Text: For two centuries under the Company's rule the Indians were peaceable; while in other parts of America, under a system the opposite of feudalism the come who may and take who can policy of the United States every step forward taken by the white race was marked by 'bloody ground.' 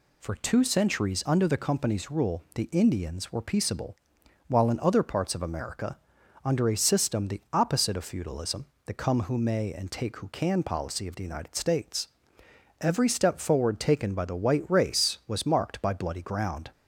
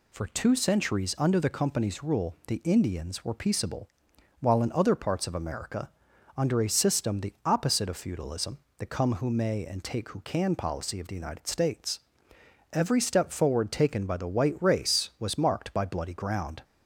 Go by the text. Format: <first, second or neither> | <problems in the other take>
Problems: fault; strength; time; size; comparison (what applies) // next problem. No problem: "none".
neither | pauses between "feudalism" and "the"; slight; the same in both // pauses between "States" and "every"; noticeable; the same in both